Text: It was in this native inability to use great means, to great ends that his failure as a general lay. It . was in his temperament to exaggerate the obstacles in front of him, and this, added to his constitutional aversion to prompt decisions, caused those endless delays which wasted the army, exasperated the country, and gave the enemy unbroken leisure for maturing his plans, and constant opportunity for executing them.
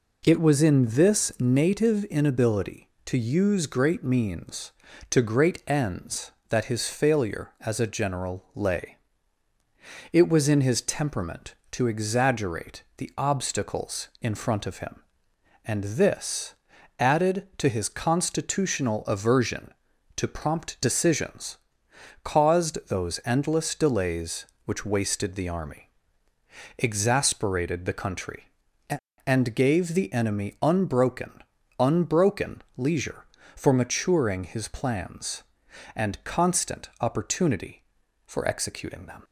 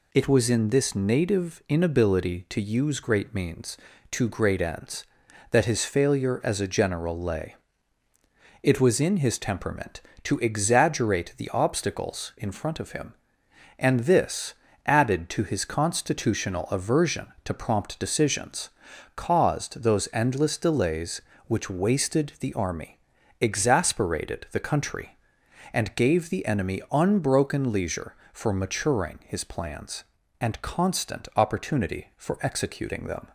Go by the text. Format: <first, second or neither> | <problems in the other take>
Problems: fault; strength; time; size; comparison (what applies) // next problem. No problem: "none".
second | says "unbroken" twice; at 31.7 s